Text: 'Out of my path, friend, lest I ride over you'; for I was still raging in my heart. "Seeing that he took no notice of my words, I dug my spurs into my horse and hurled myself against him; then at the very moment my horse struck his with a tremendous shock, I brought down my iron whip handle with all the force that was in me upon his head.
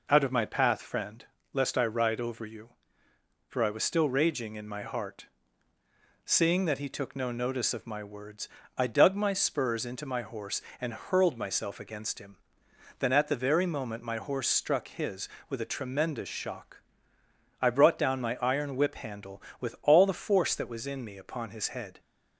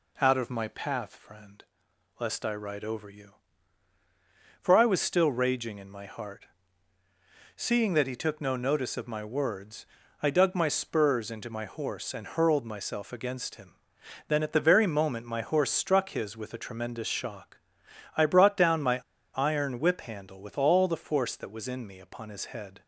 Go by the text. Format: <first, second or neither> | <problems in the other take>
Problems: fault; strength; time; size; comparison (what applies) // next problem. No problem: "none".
first | pauses between "my" and "iron"; at 19.0 s; 0.36 s long